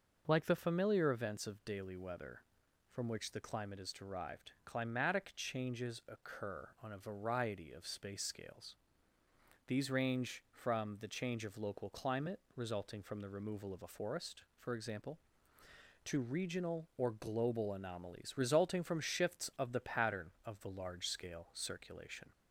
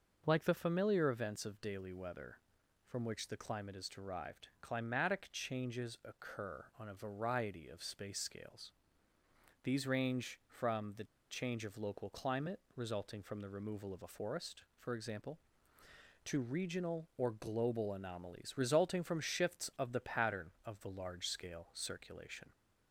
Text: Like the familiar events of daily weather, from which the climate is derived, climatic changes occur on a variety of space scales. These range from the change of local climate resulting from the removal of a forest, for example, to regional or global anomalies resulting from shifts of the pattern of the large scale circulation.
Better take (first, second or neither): first